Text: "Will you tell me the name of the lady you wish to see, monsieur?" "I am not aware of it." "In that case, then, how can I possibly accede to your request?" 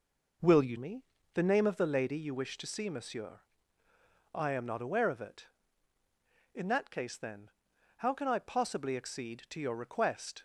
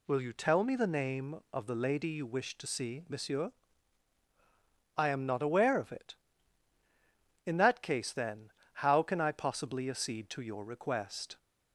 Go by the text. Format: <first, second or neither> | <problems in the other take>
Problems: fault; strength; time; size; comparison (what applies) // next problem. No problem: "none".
second | skips "tell"; at 0.7 s // pauses between "me" and "the"; slight; at 1.0 s; 0.30 s long